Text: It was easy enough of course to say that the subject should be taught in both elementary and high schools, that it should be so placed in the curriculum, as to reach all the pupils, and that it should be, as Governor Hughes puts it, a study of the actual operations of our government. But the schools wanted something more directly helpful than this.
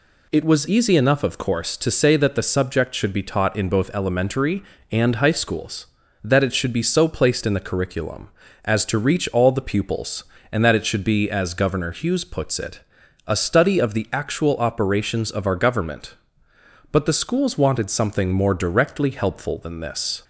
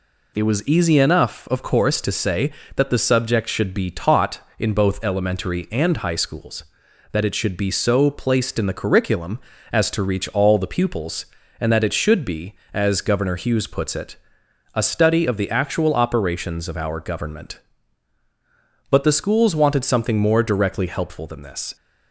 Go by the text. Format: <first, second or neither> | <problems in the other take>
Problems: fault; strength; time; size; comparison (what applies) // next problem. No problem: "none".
neither | none